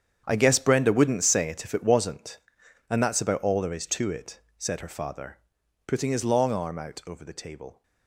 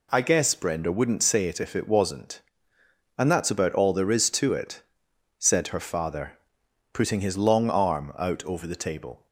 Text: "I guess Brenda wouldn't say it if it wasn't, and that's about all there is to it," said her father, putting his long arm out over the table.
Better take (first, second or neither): second